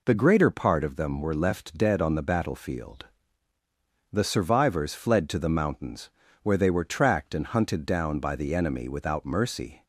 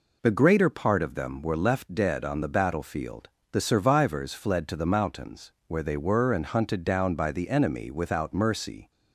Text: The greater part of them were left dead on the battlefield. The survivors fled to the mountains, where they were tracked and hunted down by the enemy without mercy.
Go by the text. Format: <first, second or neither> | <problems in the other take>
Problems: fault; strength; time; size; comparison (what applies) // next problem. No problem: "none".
first | skips "tracked"; at 6.3 s